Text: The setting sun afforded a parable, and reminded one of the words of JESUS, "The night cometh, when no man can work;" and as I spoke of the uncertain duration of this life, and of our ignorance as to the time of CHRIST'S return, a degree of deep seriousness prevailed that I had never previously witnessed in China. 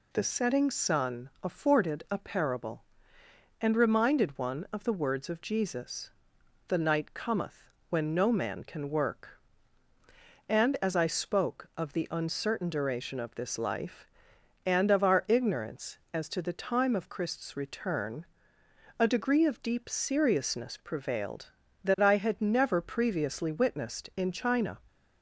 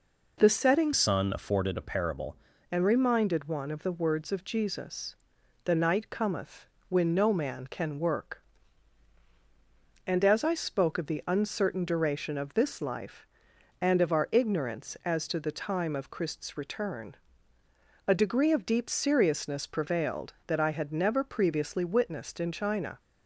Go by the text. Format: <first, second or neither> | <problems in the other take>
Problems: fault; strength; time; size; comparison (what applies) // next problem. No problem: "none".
first | changes voice from "sun" to "parable"; from 0.9 to 2.3 s; 1.4 s long